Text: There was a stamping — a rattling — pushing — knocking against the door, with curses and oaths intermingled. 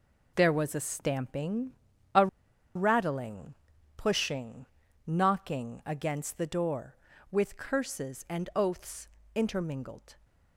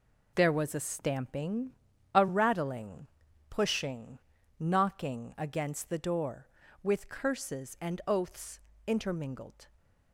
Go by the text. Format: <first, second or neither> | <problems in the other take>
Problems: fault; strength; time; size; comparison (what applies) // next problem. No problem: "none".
second | pauses between "a" and "rattling"; noticeable; at 2.2 s; 0.48 s long // pauses between "oaths" and "intermingled"; slight; at 9.0 s; 0.28 s long; slight in the second